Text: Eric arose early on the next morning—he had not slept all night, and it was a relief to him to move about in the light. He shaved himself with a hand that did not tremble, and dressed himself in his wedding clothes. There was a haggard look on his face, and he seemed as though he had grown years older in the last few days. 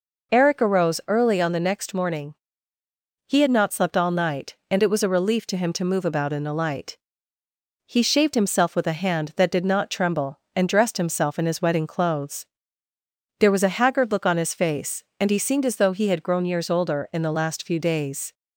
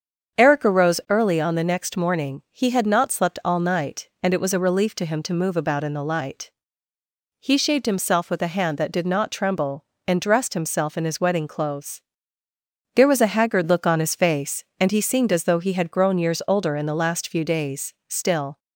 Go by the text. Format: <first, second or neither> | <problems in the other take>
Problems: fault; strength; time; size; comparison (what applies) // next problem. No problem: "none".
first | starts louder than the rest; strong; until 1.4 s; 7 dB // goes on to say "Still"; from 18.0 s on; 0.50 s long